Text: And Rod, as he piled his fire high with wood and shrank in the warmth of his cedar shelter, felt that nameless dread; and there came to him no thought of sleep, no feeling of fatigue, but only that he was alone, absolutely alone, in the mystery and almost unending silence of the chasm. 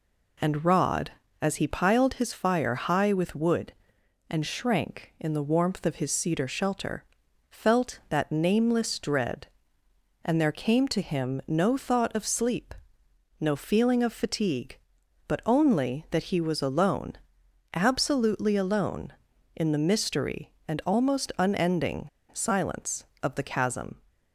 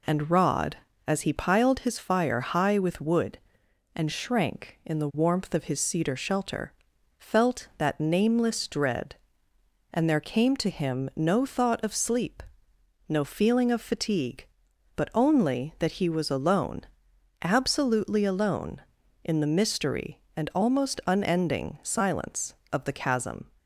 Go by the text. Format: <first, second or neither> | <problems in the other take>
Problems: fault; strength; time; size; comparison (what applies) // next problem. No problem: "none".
second | pauses between "unending" and "silence"; slight; at 22.0 s; 0.24 s long